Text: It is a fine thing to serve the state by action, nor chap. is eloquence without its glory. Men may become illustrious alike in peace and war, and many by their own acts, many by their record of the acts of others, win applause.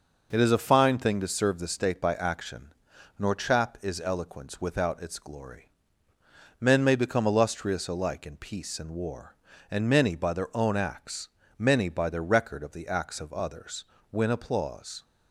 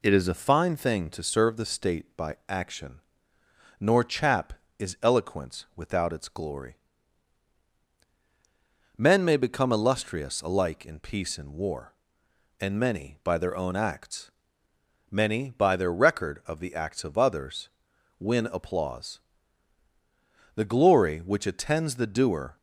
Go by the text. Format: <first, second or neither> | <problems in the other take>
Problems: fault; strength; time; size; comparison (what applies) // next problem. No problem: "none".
first | goes on to say "The glory which attends the doer"; strong; from 20.5 s on; 2.0 s long